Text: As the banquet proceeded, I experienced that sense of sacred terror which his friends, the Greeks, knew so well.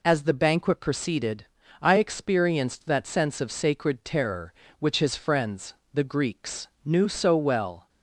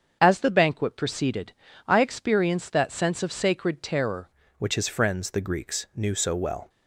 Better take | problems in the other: first | starts louder than the rest; strong; until 1.2 s; 7.5 dB // changes voice at "which"; from 4.5 s on; 2.1 s long

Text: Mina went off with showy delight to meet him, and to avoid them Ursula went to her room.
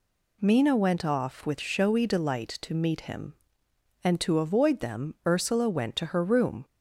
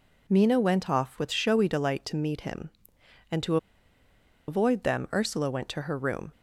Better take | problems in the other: first | pauses between "to" and "avoid"; noticeable; at 3.5 s; 0.91 s long

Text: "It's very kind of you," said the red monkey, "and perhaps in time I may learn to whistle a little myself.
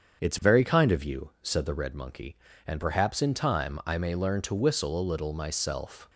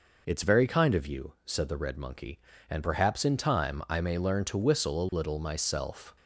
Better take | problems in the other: second | starts louder than the rest; strong; until 1.9 s; 7.5 dB

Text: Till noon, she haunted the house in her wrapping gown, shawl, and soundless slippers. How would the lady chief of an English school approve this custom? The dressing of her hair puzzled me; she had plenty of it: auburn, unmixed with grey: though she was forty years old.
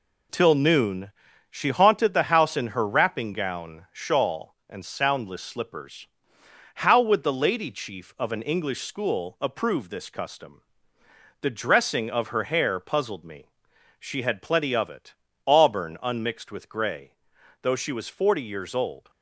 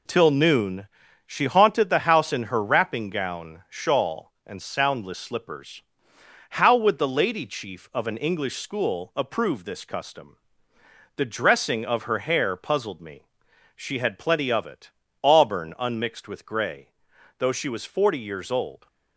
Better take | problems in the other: neither | none

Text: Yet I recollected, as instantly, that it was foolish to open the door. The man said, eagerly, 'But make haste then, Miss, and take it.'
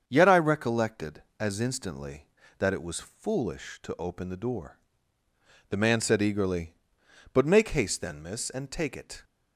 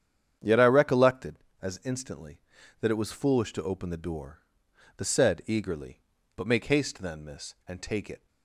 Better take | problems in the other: first | starts louder than the rest; strong; until 1.6 s; 8.5 dB; strong in the first // skips "man"; at 5.0 s

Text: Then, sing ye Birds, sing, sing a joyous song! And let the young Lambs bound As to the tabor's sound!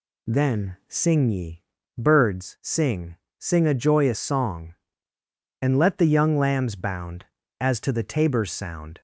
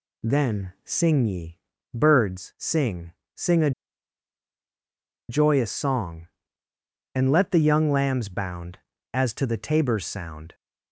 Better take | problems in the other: first | pauses between "ye" and "Birds"; slight; at 1.5 s; 0.34 s long; slight in the first // pauses between "a" and "joyous"; strong; at 3.7 s; 1.5 s long

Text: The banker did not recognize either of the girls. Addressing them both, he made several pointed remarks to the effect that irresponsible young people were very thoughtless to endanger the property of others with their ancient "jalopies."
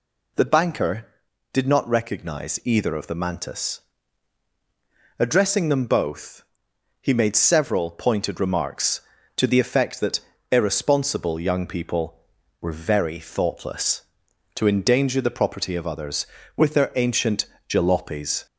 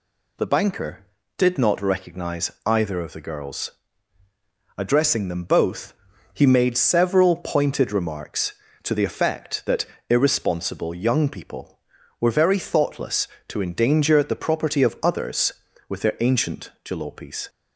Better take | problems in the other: second | says "mantis" for "girls"; at 3.1 s // pauses between "that" and "irresponsible"; slight; at 10.1 s; 0.30 s long; slight in the second // pauses between "ancient" and "jalopies"; slight; at 17.4 s; 0.22 s long

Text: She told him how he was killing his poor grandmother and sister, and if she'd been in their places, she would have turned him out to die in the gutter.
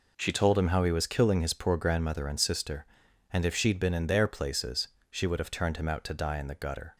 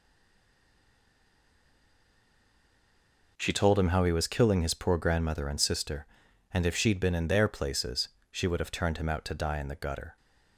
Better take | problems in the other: first | stays silent before the first word; strong; until 3.3 s; 3.3 s long

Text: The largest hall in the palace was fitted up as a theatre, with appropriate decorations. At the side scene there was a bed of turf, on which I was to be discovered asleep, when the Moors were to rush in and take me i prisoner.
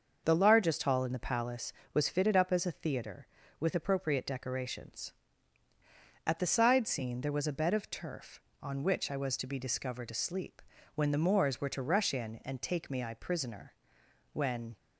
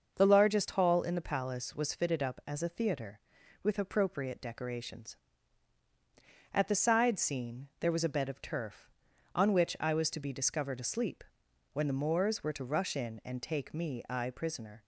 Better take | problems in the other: second | starts louder than the rest; until 1.2 s; 6.5 dB; also in the second // goes on to say "When"; slight; from 14.3 s on; 0.42 s long

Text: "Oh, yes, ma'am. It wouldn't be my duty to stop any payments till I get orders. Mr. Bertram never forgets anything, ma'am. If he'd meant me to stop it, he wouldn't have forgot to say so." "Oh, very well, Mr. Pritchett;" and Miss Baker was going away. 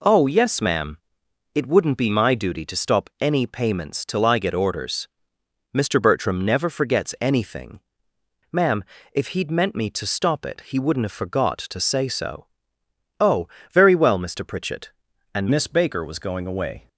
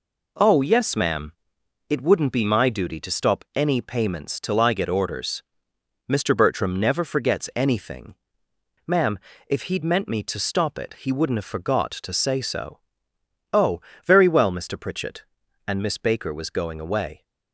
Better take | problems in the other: second | changes voice at "Miss"; from 15.4 s on; 1.4 s long

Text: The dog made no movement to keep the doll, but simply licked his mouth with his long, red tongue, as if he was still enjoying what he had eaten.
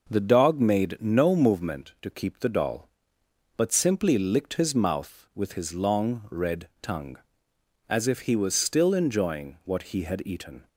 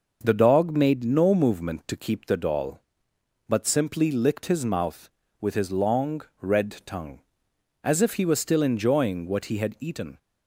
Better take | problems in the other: neither | none

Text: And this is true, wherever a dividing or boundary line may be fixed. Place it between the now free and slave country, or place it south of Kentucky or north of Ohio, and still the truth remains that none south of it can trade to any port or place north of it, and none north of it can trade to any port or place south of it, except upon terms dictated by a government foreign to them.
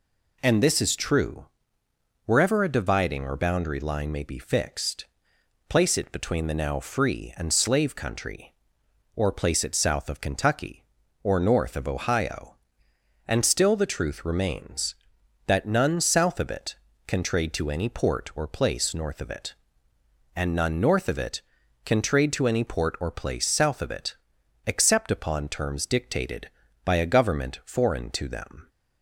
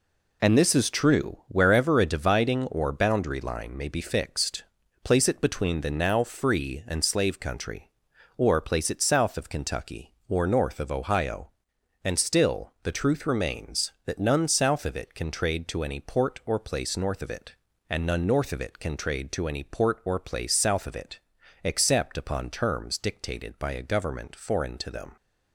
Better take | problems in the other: neither | none

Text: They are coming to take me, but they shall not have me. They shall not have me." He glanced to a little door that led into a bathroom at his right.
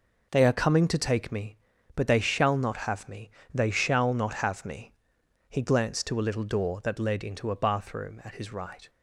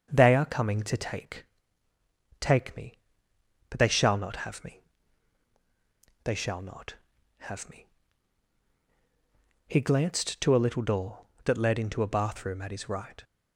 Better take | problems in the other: first | starts louder than the rest; until 1.1 s; 7 dB // says "take" twice; at 2.3 s

